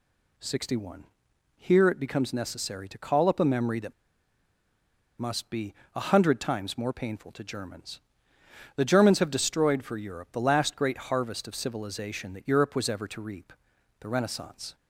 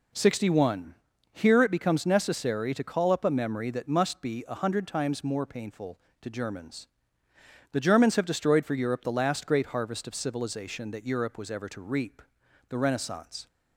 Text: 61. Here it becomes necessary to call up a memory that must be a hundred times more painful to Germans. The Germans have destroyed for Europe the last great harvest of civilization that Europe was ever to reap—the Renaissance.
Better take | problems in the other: second | pauses between "that" and "must"; strong; at 3.9 s; 1.2 s long // pauses between "be" and "a"; slight; at 5.7 s; 0.20 s long

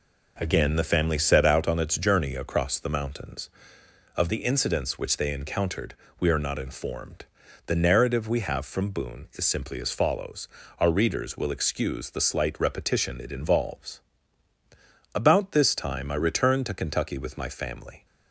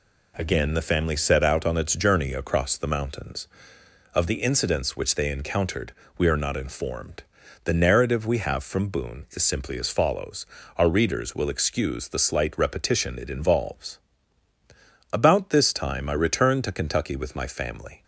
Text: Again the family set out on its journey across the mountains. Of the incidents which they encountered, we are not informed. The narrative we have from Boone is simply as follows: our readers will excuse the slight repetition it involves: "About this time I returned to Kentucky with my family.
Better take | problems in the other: second | starts louder than the rest; noticeable; until 1.9 s; 4.5 dB

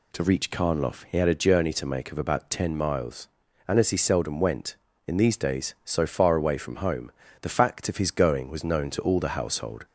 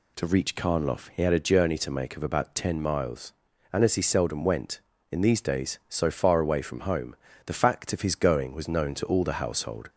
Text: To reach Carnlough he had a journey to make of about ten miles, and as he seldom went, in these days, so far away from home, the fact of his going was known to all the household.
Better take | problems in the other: neither | none

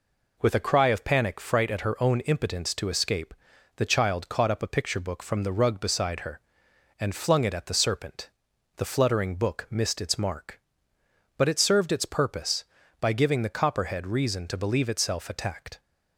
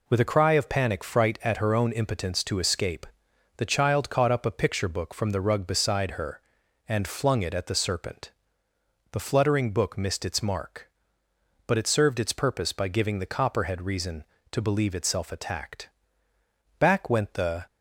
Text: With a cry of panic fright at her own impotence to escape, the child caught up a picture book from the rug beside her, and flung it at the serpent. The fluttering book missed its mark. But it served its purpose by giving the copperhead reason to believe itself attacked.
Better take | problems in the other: first | goes on to say "Back went the"; noticeable; from 16.7 s on; 0.88 s long

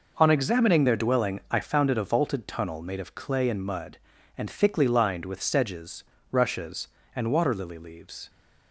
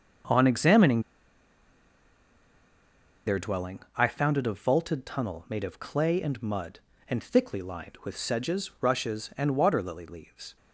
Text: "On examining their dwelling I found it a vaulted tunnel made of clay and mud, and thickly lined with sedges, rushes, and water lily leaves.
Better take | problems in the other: first | starts louder than the rest; until 3.5 s; 6.5 dB // pauses between "examining" and "their"; strong; at 1.0 s; 2.2 s long // pauses between "dwelling" and "I"; slight; at 3.7 s; 0.18 s long

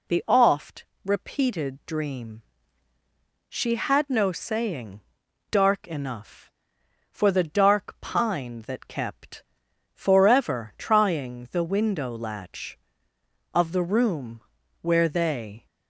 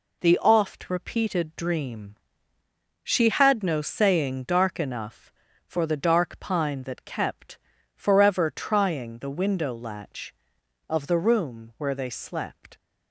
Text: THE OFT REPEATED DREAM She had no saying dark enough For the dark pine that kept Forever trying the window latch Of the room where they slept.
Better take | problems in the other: second | pauses between "OFT" and "REPEATED"; slight; at 0.8 s; 0.20 s long // pauses between "DREAM" and "She"; at 2.4 s; 1.0 s long; noticeable in the second // pauses between "saying" and "dark"; noticeable; at 5.0 s; 0.50 s long // pauses between "kept" and "Forever"; noticeable; at 9.4 s; 0.54 s long; slight in the second // pauses between "room" and "where"; at 14.4 s; 0.38 s long // stops before "slept"; at 15.6 s

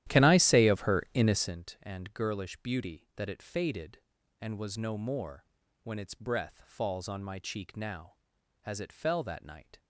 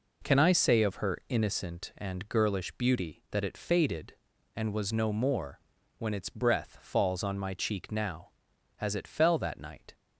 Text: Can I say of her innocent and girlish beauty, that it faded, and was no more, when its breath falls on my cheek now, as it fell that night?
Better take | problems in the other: second | starts louder than the rest; strong; until 1.6 s; 12.5 dB

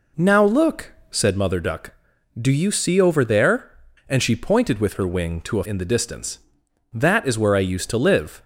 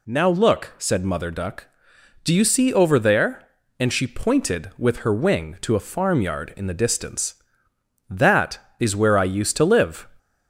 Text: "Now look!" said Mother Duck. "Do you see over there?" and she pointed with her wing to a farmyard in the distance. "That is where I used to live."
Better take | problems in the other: second | skips "farmyard"; at 5.6 s

